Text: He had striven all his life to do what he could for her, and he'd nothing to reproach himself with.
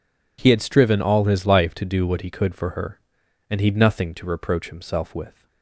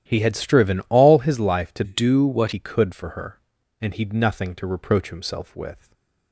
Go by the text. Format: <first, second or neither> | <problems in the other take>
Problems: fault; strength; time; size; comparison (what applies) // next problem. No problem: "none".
first | starts louder than the rest; strong; until 1.0 s; 10.5 dB // changes voice from "do" to "what"; from 1.8 to 2.5 s; 0.7 s long // stays silent after the last word; slight; from 5.7 s on; 0.6 s long